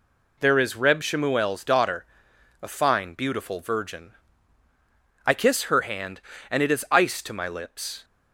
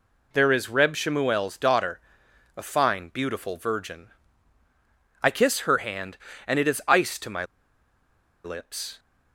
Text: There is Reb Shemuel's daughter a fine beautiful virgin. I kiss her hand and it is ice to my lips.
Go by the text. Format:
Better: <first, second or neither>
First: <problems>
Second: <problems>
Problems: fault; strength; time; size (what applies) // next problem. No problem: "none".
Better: first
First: pauses between "daughter" and "a"; noticeable; at 2.0 s; 0.54 s long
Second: pauses between "daughter" and "a"; noticeable; at 2.0 s; 0.54 s long // pauses between "my" and "lips"; at 7.4 s; 0.99 s long